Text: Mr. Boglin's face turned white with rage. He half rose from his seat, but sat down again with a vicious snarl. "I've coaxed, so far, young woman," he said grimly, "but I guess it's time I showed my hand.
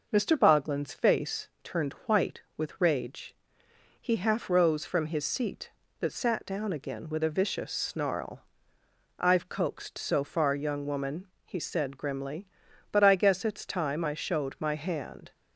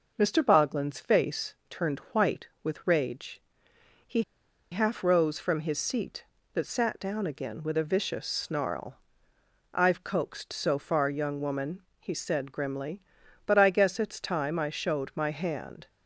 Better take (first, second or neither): first